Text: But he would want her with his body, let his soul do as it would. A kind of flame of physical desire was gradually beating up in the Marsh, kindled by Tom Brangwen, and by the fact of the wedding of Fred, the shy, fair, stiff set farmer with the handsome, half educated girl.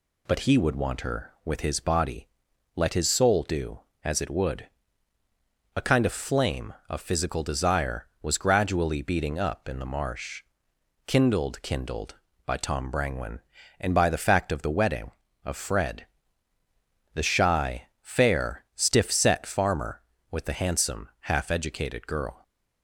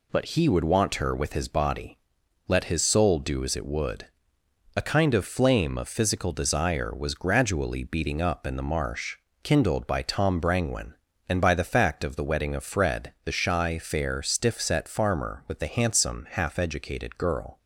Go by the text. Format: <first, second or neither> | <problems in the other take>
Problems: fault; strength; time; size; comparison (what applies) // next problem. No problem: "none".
second | says "kindled" twice; at 11.6 s